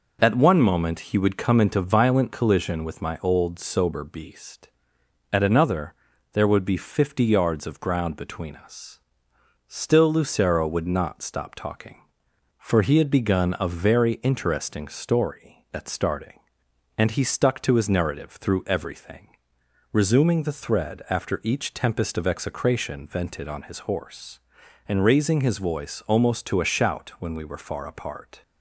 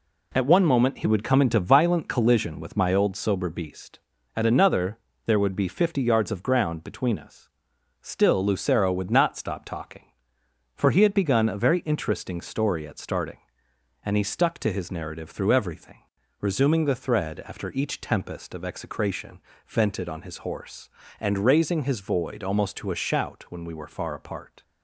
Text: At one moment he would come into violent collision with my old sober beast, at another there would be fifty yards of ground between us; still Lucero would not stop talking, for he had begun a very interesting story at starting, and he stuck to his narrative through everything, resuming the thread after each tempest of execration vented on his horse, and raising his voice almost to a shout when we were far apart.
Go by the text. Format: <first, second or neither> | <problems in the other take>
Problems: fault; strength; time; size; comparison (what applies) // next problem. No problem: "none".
first | pauses between "another" and "there"; slight; at 4.9 s; 0.30 s long; also in the first // pauses between "execration" and "vented"; slight; at 19.3 s; 0.28 s long // says "void" for "voice"; at 22.0 s